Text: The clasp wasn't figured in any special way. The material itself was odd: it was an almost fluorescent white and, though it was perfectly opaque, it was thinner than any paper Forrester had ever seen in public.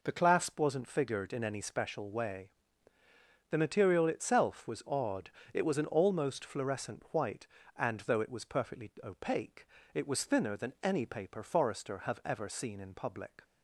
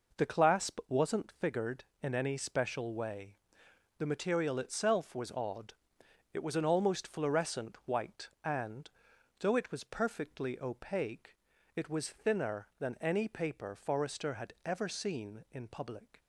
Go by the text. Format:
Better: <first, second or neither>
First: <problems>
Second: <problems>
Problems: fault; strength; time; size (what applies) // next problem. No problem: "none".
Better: second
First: says "have" for "had"; at 11.9 s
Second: none